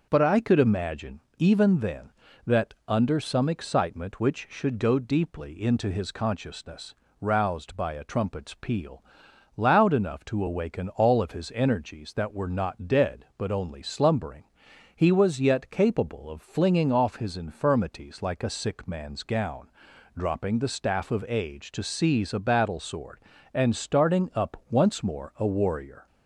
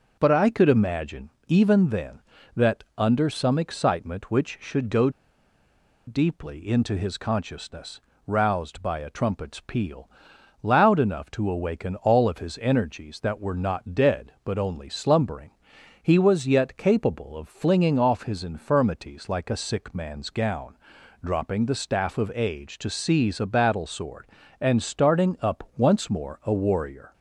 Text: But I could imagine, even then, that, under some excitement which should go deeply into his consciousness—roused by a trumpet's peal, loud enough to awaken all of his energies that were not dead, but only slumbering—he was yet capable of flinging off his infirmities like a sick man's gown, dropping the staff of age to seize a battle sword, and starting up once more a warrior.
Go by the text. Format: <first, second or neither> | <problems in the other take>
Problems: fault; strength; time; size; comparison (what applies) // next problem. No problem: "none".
first | pauses between "go" and "deeply"; noticeable; at 5.0 s; 0.97 s long